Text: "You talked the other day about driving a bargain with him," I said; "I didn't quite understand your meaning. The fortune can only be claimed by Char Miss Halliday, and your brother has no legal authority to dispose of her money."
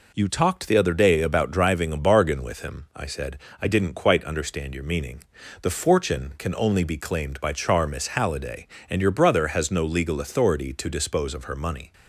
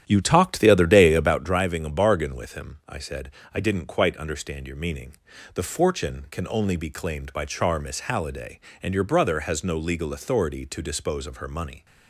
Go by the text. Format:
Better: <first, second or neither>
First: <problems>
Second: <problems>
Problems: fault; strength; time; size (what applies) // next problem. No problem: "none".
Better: first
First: none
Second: starts louder than the rest; strong; until 1.5 s; 10.5 dB